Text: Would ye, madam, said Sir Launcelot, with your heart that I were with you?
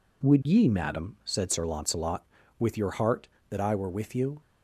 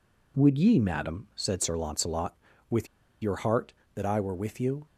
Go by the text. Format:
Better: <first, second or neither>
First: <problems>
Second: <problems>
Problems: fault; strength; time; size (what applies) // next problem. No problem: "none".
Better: first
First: none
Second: pauses between "with" and "your"; at 2.8 s; 0.36 s long